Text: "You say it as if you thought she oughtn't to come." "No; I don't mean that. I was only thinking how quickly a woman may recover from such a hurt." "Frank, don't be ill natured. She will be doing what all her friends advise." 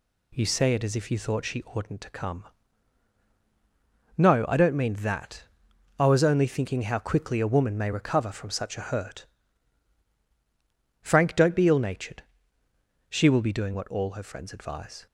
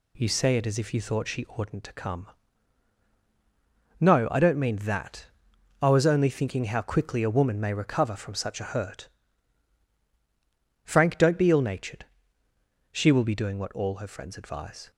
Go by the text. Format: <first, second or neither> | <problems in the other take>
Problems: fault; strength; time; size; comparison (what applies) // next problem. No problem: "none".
neither | none